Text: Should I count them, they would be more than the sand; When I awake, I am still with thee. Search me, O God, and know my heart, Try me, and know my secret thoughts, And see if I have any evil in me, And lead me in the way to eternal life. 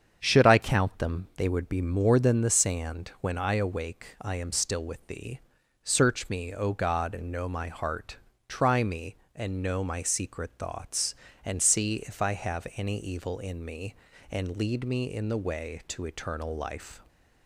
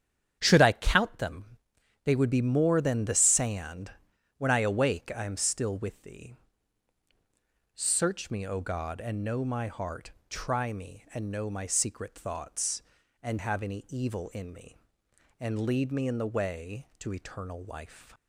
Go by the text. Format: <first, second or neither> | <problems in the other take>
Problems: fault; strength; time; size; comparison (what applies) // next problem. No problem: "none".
first | starts louder than the rest; strong; until 1.4 s; 8.5 dB; strong in the first // skips "see if I"; at 13.3 s